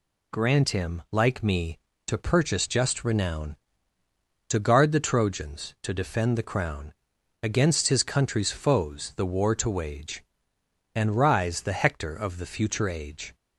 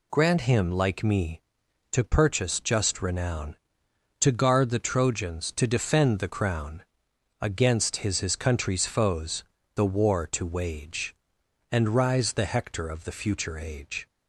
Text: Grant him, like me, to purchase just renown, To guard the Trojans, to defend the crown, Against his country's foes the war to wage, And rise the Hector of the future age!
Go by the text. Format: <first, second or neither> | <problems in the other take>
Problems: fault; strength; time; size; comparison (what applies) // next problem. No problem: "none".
first | says "his" twice; at 8.1 s // pauses between "foes" and "the"; slight; at 9.4 s; 0.32 s long